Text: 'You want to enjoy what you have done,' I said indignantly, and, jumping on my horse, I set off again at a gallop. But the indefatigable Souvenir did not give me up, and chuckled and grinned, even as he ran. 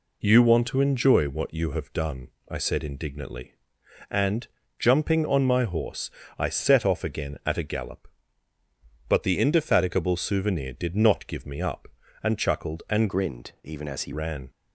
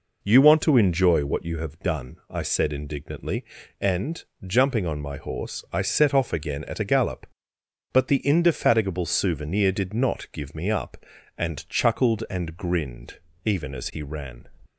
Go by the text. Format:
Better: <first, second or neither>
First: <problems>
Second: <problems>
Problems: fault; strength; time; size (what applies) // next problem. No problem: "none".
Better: second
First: changes voice from "grinned" to "he"; from 13.0 to 14.1 s; 1.1 s long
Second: none